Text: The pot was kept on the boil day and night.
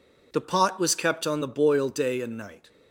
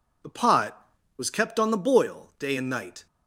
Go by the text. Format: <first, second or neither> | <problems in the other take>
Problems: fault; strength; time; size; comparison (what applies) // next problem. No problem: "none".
neither | none